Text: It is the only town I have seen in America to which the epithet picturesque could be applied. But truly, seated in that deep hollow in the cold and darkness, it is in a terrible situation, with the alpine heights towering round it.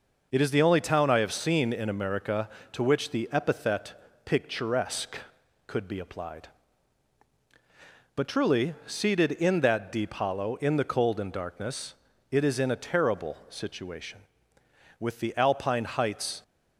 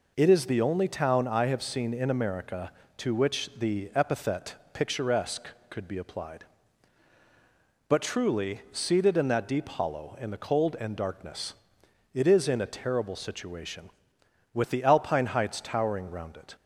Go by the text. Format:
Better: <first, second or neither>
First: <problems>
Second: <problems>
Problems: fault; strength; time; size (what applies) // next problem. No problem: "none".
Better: second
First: pauses between "epithet" and "picturesque"; slight; at 3.9 s; 0.32 s long // stops before "towering round it"; at 16.4 s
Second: pauses between "epithet" and "picturesque"; slight; at 4.5 s; 0.18 s long